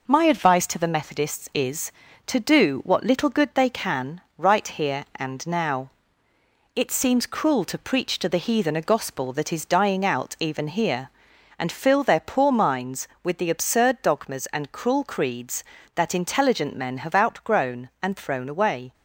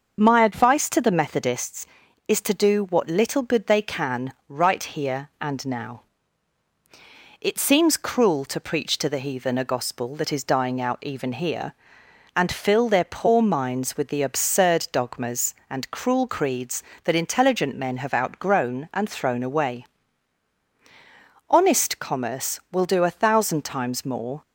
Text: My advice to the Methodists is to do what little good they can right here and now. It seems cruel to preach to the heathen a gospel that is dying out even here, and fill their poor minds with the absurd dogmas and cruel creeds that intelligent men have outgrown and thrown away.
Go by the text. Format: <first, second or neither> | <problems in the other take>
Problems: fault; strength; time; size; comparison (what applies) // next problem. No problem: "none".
first | starts louder than the rest; until 1.2 s; 6.5 dB // pauses between "can" and "right"; slight; at 4.3 s; 0.16 s long; slight in the first // goes on to say "Honest commerce will do a thousand times more"; strong; from 21.4 s on; 2.9 s long